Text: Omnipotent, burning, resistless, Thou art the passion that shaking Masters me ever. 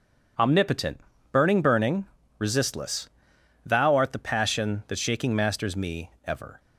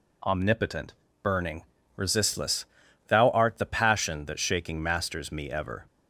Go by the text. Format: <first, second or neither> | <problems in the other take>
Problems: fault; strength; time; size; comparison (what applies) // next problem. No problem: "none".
second | says "burning" twice; at 1.6 s // pauses between "me" and "ever"; slight; at 6.0 s; 0.16 s long